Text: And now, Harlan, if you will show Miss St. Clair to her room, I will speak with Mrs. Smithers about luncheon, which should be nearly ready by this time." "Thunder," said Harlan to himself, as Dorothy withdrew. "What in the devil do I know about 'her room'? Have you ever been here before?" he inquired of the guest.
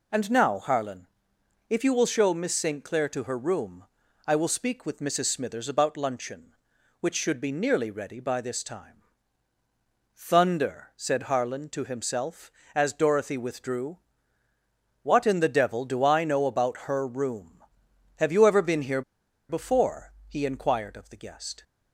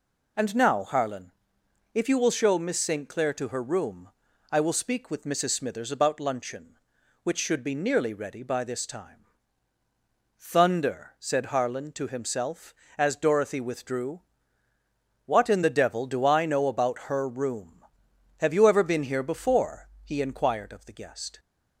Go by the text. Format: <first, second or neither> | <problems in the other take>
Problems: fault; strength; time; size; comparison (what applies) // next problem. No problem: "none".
second | pauses between "here" and "before"; noticeable; at 19.0 s; 0.47 s long